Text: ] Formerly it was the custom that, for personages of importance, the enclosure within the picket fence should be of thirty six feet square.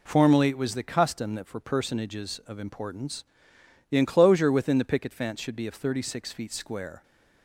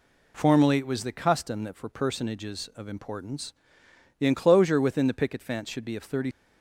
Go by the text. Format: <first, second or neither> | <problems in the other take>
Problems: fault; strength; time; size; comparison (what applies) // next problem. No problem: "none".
first | stops before "six feet square"; at 6.3 s